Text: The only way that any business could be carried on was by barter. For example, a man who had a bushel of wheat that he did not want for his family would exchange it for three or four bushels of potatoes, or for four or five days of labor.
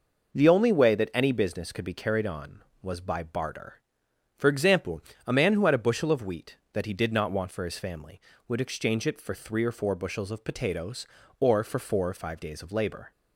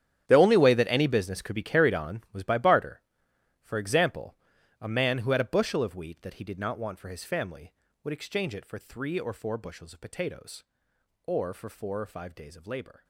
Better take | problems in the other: first | gets quieter; strong; throughout; 16.5 dB

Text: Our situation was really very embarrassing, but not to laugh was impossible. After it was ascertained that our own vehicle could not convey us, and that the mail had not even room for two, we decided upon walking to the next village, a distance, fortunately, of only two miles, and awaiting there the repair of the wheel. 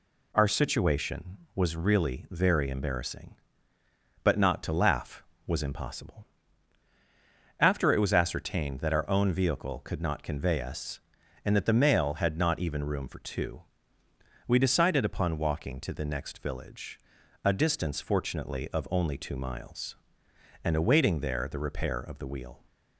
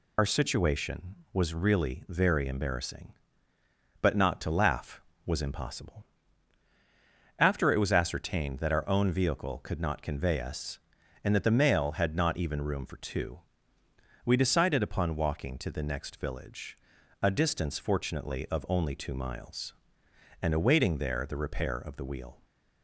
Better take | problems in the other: first | loses the start of "Our"; at 0.1 s; 60 ms

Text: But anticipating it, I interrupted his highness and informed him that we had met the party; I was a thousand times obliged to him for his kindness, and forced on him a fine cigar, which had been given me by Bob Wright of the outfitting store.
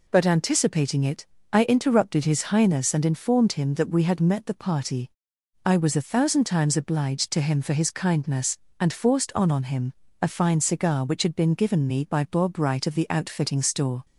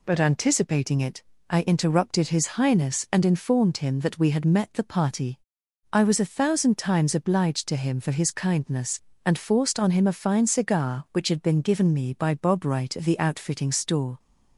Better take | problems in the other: second | says "on" twice; at 9.5 s // pauses between "him" and "a"; slight; at 9.9 s; 0.30 s long

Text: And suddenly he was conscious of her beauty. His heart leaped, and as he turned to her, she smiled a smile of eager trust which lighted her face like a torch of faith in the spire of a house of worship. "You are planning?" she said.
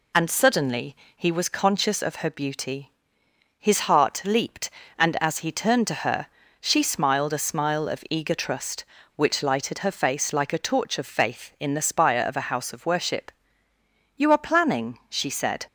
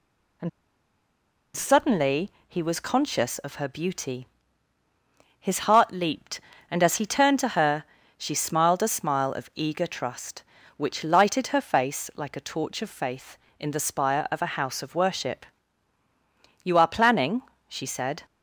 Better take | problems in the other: first | pauses between "And" and "suddenly"; at 0.4 s; 1.0 s long // pauses between "suddenly" and "he"; slight; at 2.2 s; 0.18 s long; slight in the first

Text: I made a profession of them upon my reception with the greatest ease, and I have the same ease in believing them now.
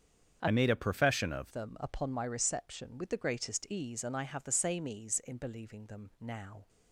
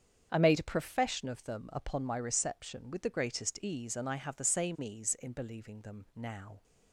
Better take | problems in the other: second | starts louder than the rest; strong; until 1.4 s; 8 dB; strong in the second // changes voice from "made" to "of"; from 0.5 to 1.5 s; 1.0 s long

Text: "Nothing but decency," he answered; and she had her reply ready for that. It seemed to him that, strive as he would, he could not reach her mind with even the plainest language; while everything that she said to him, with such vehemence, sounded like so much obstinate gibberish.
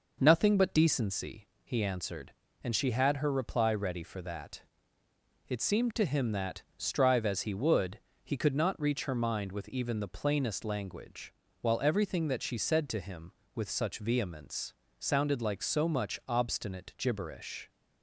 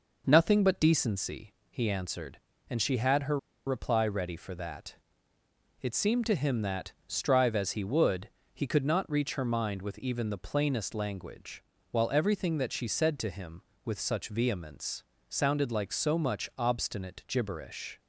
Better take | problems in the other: first | pauses between "her" and "reply"; slight; at 3.3 s; 0.29 s long

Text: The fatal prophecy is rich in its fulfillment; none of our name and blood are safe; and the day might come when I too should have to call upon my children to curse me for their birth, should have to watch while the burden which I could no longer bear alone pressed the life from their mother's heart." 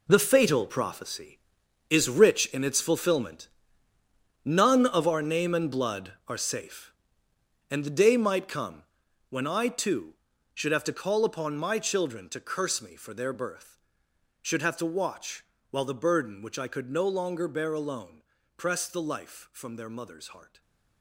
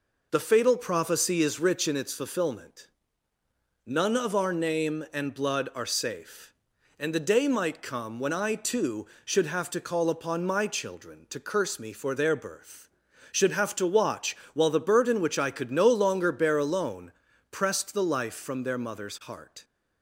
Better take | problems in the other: second | gets quieter; strong; throughout; 11.5 dB // pauses between "come" and "when"; noticeable; at 8.8 s; 0.48 s long // pauses between "watch" and "while"; slight; at 15.4 s; 0.30 s long; slight in the second // pauses between "alone" and "pressed"; slight; at 18.2 s; 0.34 s long; also in the second // stays silent after the last word; slight; from 20.4 s on; 0.6 s long

